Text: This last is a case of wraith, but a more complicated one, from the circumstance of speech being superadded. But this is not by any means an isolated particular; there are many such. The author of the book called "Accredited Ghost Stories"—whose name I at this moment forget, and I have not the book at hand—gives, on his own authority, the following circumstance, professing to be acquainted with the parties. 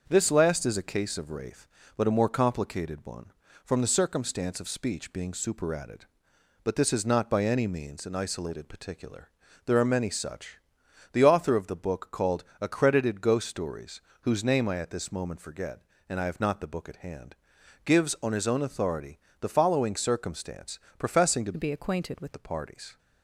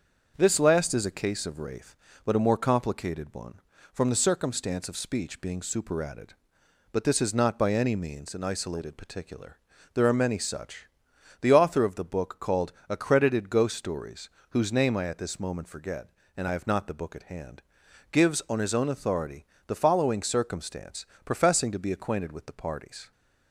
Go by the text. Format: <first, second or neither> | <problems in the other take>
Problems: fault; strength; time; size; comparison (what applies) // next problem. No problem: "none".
second | starts louder than the rest; until 1.0 s; 6.5 dB; also in the second // pauses between "called" and "Accredited"; slight; at 12.4 s; 0.16 s long; slight in the second // changes voice from "be" to "with"; from 21.5 to 22.3 s; 0.8 s long